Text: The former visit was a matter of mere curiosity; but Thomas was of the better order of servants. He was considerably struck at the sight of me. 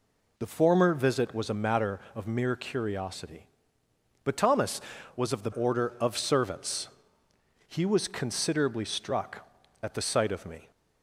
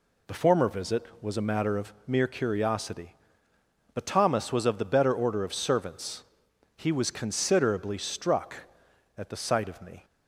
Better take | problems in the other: second | skips "better"; at 5.5 s

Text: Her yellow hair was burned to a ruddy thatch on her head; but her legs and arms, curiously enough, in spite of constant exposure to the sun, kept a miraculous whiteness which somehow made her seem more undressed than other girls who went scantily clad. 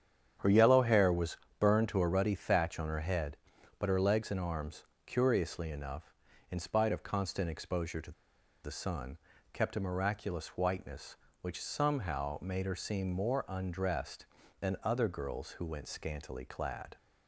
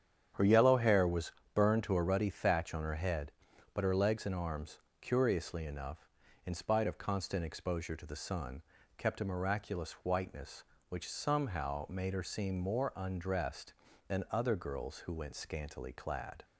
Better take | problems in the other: second | starts louder than the rest; strong; until 1.6 s; 8.5 dB; strong in the second // pauses between "was" and "burned"; slight; at 1.3 s; 0.22 s long; slight in the second // pauses between "to" and "the"; noticeable; at 8.1 s; 0.52 s long

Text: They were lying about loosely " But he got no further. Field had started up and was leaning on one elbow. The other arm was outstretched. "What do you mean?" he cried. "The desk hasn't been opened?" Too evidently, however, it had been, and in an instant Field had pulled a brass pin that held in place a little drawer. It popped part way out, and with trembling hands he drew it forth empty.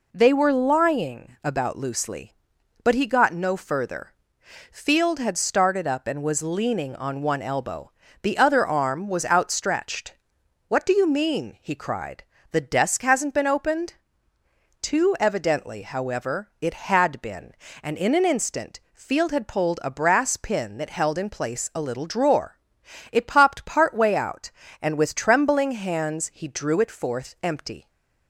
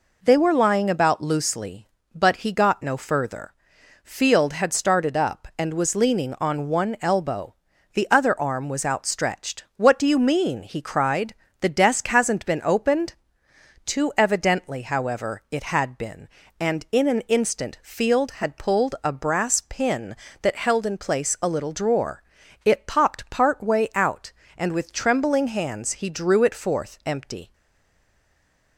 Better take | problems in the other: first | stays silent after the last word; noticeable; from 27.5 s on; 1.2 s long

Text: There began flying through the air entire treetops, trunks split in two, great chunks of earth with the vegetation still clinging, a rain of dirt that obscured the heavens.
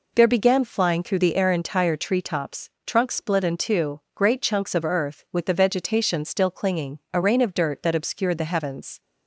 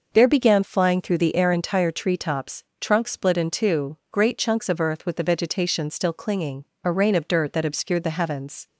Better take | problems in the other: neither | none

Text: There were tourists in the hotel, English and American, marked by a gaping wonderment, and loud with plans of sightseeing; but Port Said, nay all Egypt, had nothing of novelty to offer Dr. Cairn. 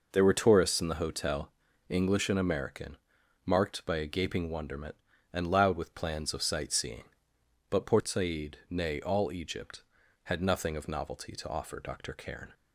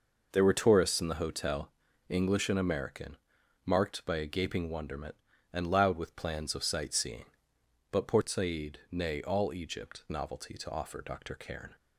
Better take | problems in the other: first | skips "had nothing of"; at 10.0 s

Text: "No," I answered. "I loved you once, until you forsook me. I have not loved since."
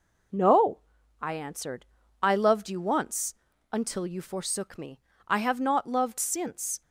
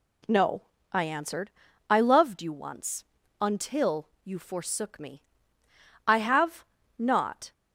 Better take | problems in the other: first | pauses between "until" and "you"; slight; at 4.0 s; 0.16 s long // pauses between "have" and "not"; slight; at 6.6 s; 0.34 s long // stops before "loved since"; at 7.5 s

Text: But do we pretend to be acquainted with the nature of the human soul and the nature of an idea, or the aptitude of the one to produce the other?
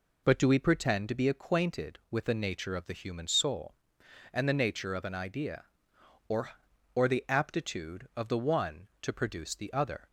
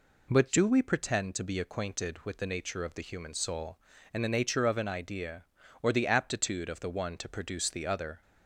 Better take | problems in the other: second | says "or" twice; at 6.9 s

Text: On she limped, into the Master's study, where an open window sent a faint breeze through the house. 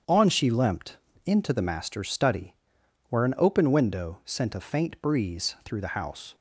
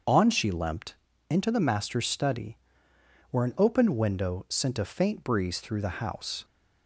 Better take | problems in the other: neither | starts louder than the rest; the same in both

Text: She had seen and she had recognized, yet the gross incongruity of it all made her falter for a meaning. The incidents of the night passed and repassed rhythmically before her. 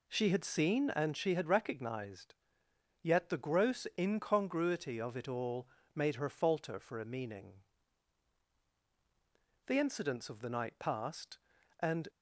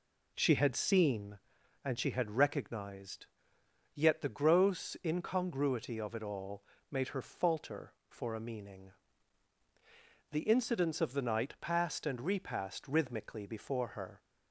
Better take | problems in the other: second | pauses between "all" and "made"; slight; at 5.6 s; 0.28 s long; slight in the second // stops before "repassed rhythmically before her"; at 12.0 s

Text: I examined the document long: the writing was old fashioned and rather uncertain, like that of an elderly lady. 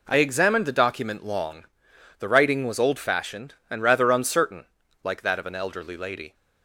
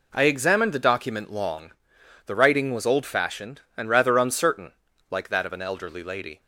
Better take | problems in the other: neither | none

